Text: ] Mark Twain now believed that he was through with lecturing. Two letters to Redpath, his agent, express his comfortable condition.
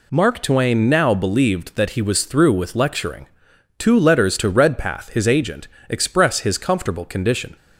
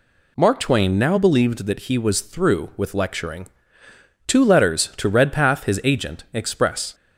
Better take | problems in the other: first | stops before "his comfortable condition"; at 6.9 s

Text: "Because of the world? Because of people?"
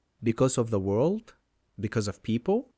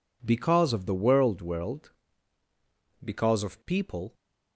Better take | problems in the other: first | says "world" twice; at 1.4 s

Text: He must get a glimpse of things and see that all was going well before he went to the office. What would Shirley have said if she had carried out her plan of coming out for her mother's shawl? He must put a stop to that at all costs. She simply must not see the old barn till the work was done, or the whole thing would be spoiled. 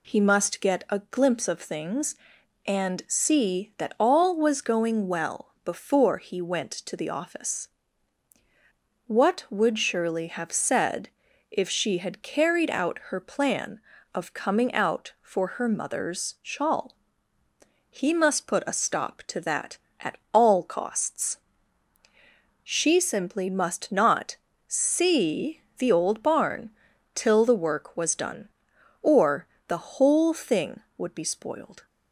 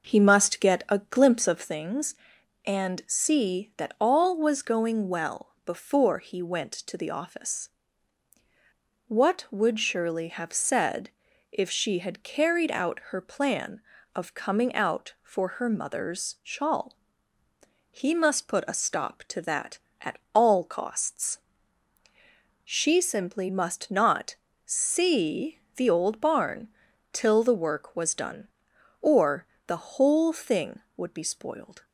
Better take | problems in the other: first | starts louder than the rest; noticeable; until 1.8 s; 5.5 dB // pauses between "said" and "if"; at 11.0 s; 0.42 s long; also in the first // pauses between "at" and "all"; slight; at 20.1 s; 0.16 s long; slight in the first // pauses between "not" and "see"; slight; at 24.3 s; 0.30 s long; slight in the first // pauses between "see" and "the"; slight; at 25.6 s; 0.16 s long; slight in the first // pauses between "barn" and "till"; noticeable; at 26.6 s; 0.46 s long; noticeable in the first // pauses between "or" and "the"; slight; at 29.4 s; 0.22 s long; slight in the first

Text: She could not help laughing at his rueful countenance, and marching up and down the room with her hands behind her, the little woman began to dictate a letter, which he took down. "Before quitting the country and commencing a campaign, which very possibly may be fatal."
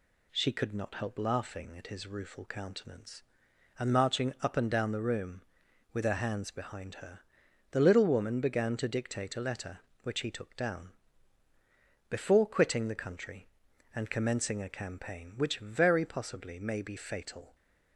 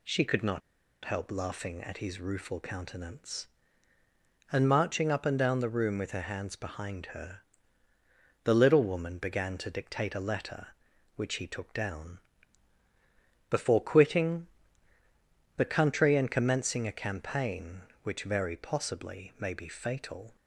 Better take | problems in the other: first | pauses between "not" and "help"; at 0.6 s; 0.44 s long // pauses between "quitting" and "the"; at 14.4 s; 1.1 s long

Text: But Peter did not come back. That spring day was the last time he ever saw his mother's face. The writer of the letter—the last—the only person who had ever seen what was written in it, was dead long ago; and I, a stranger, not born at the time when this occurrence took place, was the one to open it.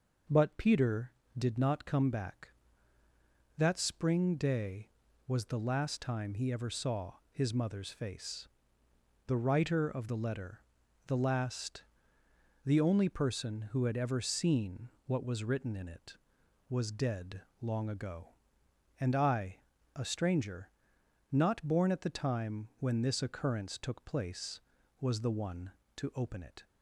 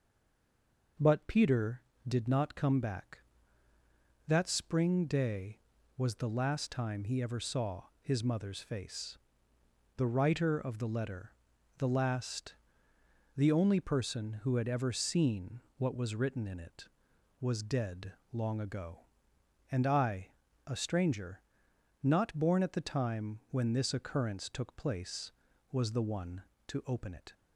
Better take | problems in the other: first | stays silent before the first word; until 0.9 s; 0.9 s long // pauses between "saw" and "his"; slight; at 7.8 s; 0.18 s long; slight in the first // pauses between "seen" and "what"; slight; at 15.6 s; 0.16 s long; slight in the first // pauses between "dead" and "long"; slight; at 18.1 s; 0.18 s long; slight in the first

